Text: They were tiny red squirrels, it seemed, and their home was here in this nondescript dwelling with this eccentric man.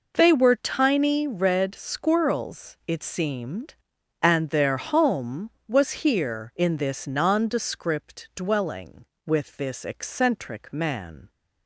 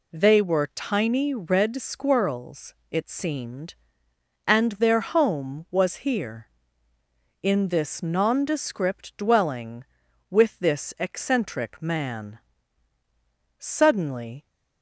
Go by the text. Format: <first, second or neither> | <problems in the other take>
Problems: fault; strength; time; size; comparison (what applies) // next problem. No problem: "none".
first | goes on to say "Suddenly"; noticeable; from 13.5 s on; 0.88 s long